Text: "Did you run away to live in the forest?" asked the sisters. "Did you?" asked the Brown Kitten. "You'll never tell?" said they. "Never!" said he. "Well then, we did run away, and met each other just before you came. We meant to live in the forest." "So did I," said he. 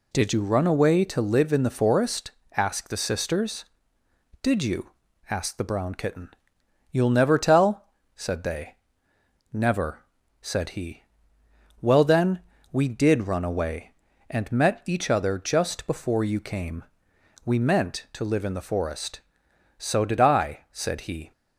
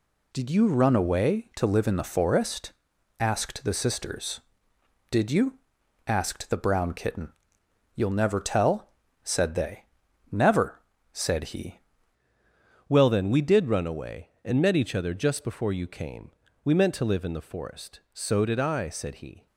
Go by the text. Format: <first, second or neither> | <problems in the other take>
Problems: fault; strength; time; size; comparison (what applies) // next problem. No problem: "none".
first | changes voice at "Well"; from 12.9 s on; 6.5 s long